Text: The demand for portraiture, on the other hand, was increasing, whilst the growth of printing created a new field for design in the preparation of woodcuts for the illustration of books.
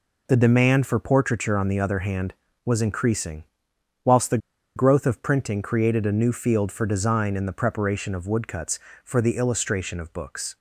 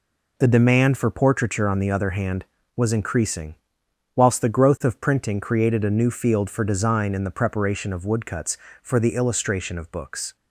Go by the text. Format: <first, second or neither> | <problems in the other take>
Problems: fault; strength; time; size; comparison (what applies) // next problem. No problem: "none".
second | pauses between "the" and "growth"; at 4.3 s; 0.38 s long